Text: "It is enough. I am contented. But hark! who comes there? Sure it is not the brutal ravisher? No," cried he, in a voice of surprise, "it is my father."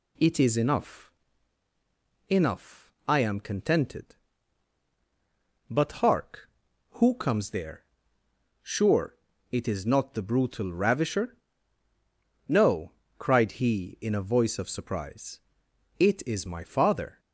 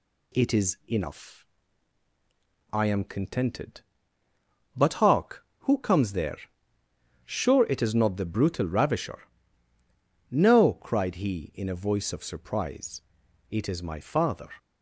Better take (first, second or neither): second